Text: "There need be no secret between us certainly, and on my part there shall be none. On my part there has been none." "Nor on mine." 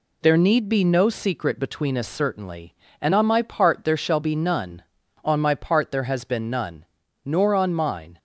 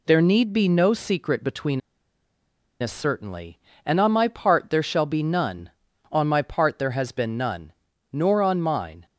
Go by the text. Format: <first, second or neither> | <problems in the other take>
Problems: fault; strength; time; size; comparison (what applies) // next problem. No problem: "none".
first | pauses between "between" and "us"; at 1.8 s; 1.0 s long